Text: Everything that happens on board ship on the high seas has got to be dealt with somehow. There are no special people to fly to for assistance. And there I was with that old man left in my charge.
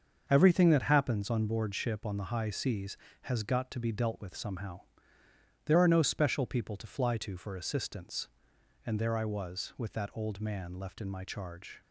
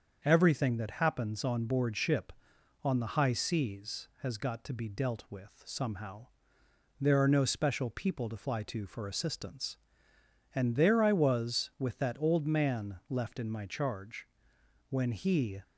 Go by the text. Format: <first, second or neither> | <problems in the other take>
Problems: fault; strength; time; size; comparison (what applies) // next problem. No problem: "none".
first | starts louder than the rest; until 1.2 s; 7 dB; also in the first // goes on to say "When he"; noticeable; from 14.8 s on; 0.72 s long